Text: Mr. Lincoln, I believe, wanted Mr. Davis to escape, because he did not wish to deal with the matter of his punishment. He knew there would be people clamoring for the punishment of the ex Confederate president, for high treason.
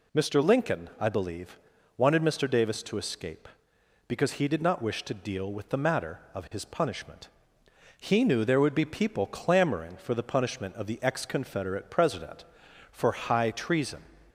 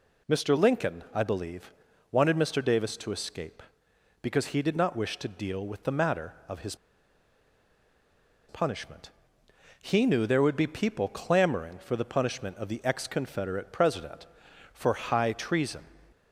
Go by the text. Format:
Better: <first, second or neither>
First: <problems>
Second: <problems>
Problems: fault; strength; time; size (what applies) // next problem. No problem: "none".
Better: first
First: none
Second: pauses between "his" and "punishment"; strong; at 6.7 s; 1.7 s long